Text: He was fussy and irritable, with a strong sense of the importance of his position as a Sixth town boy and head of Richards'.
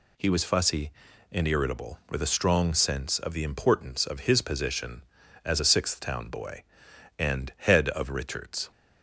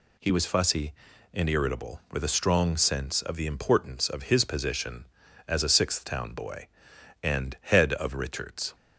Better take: neither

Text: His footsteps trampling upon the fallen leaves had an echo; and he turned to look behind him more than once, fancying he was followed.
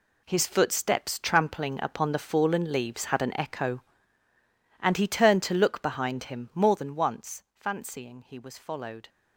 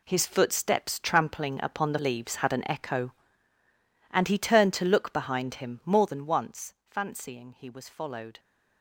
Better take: first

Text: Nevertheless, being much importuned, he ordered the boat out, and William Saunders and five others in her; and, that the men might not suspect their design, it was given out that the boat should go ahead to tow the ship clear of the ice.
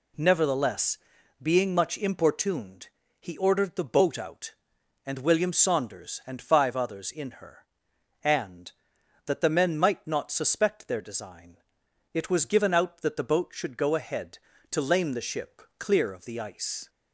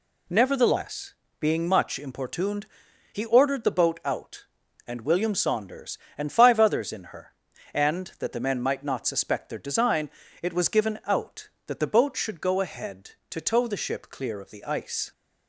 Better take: second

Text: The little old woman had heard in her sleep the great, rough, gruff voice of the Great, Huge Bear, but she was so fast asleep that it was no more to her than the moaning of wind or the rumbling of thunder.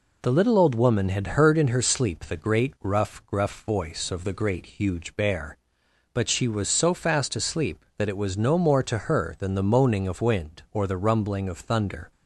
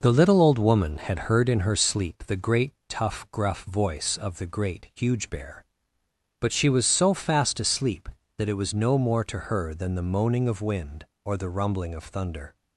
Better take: first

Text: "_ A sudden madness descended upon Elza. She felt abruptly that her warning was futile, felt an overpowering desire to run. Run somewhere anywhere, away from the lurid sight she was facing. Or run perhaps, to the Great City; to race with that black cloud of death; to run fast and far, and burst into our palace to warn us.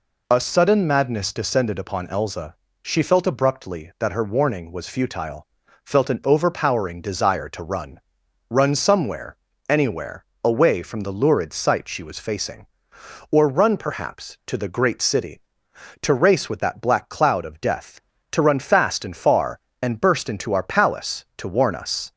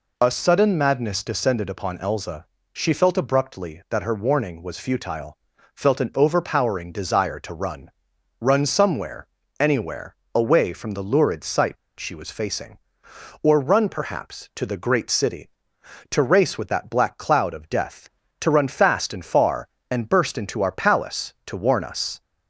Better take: first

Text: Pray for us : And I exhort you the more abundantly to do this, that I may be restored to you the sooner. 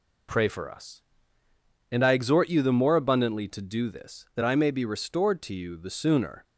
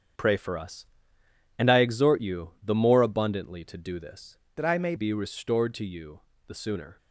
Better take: first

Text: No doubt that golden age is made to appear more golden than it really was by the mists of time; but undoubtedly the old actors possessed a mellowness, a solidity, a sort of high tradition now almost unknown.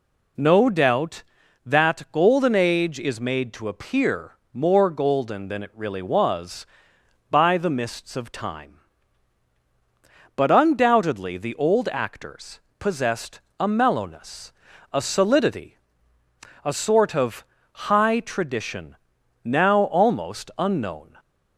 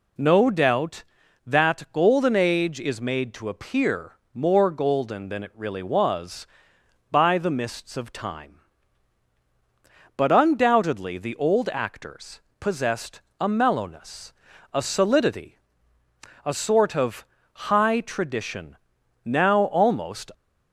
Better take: first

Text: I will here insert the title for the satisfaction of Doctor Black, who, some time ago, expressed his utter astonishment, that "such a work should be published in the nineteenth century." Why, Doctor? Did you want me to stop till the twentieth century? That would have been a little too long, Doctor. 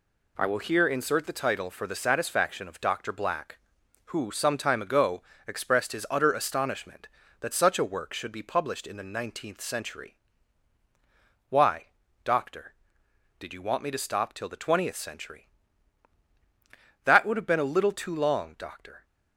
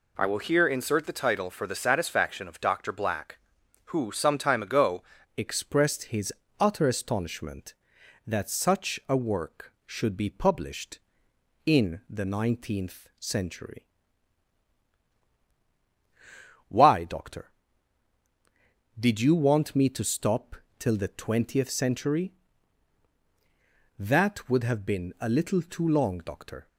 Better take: first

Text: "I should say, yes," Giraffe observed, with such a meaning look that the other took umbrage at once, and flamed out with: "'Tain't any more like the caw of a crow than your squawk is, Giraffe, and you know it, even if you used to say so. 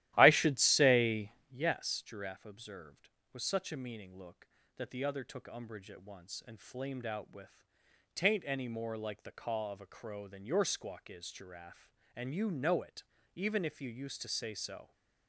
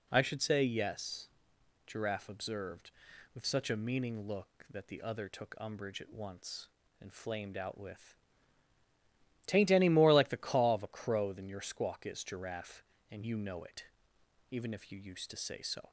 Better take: second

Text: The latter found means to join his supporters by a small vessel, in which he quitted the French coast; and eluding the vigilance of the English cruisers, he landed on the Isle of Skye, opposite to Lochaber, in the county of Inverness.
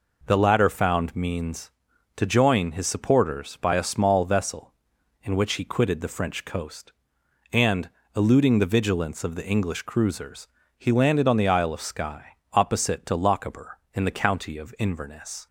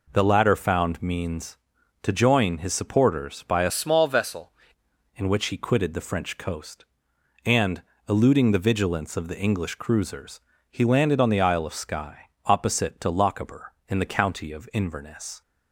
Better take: first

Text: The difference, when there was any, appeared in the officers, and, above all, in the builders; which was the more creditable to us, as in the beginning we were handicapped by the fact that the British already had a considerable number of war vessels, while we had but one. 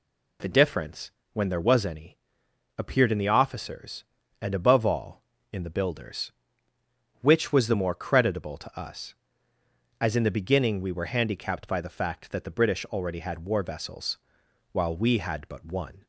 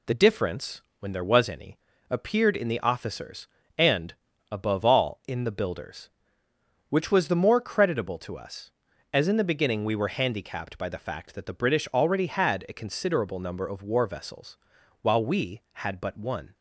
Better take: second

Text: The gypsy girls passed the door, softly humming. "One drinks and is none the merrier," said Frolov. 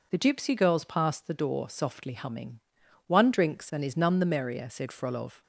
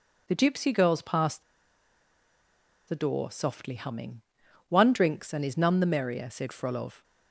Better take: first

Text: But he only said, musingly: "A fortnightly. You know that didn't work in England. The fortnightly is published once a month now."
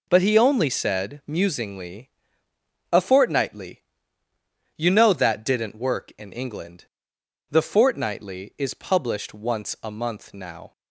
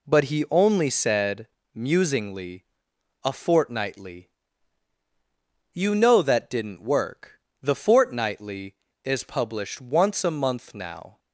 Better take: first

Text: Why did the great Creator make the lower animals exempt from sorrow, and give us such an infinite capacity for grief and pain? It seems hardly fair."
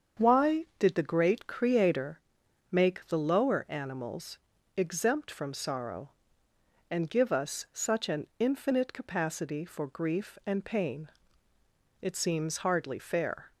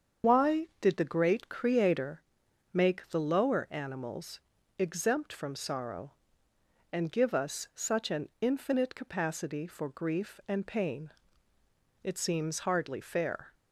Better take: first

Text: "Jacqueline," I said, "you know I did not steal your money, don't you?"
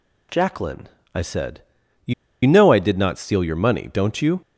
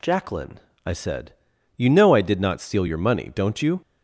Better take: second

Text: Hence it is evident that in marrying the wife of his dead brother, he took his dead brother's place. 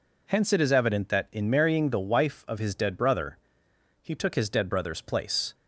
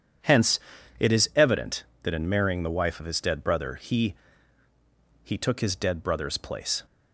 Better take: first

